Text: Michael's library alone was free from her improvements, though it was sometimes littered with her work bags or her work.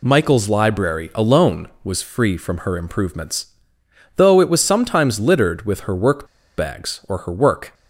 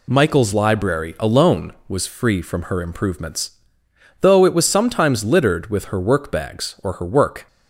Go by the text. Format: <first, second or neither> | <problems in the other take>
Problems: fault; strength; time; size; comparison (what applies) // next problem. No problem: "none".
second | pauses between "work" and "bags"; slight; at 6.2 s; 0.30 s long